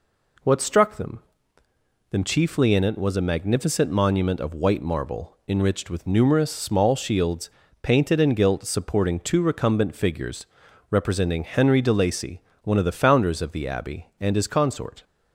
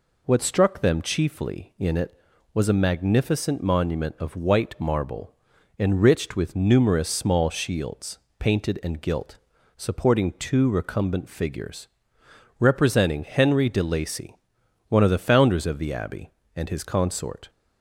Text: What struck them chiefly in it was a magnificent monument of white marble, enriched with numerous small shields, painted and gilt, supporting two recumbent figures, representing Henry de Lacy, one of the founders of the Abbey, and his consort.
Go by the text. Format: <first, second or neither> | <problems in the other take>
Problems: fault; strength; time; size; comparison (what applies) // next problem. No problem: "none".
second | says "them" twice; at 2.0 s